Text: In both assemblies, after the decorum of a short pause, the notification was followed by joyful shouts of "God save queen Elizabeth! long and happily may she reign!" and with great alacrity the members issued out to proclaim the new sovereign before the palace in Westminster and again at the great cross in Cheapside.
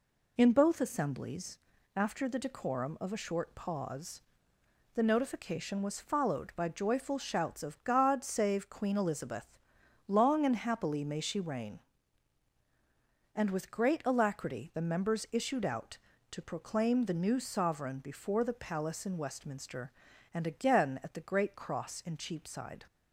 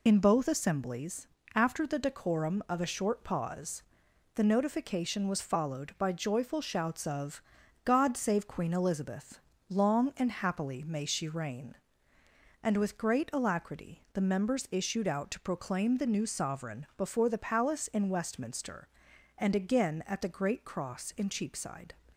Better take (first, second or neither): first